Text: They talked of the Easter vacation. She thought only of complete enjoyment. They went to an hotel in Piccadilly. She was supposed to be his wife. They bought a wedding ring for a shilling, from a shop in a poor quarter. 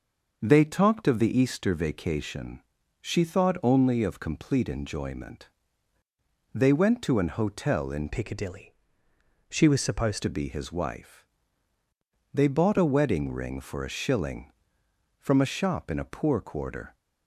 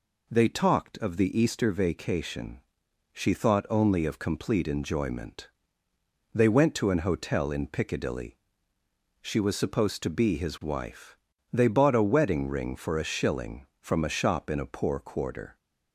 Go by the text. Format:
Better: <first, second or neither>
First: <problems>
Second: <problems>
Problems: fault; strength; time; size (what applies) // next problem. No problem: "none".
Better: second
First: starts louder than the rest; until 1.4 s; 6 dB // changes voice from "Piccadilly" to "supposed"; from 8.1 to 10.2 s; 2.1 s long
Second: none